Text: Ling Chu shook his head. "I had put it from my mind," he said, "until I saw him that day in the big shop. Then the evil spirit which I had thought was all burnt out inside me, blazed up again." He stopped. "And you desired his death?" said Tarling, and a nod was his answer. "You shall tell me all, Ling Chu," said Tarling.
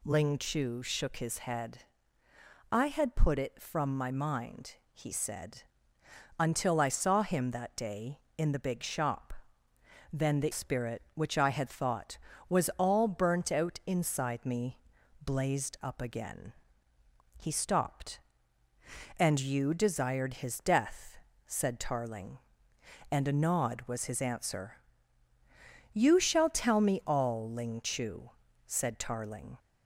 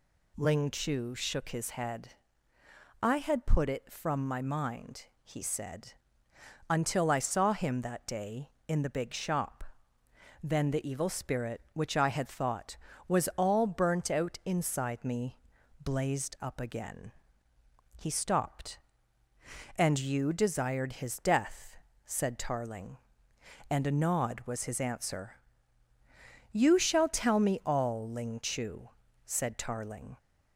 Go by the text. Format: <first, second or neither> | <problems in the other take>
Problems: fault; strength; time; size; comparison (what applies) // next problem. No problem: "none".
second | skips "evil"; at 10.5 s